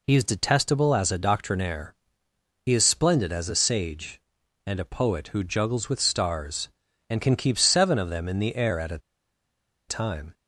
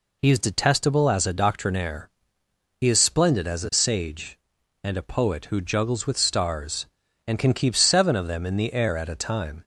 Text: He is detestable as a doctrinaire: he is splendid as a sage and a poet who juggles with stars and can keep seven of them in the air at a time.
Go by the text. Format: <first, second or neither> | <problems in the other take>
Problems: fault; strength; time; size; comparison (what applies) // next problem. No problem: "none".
second | pauses between "a" and "time"; noticeable; at 8.9 s; 0.90 s long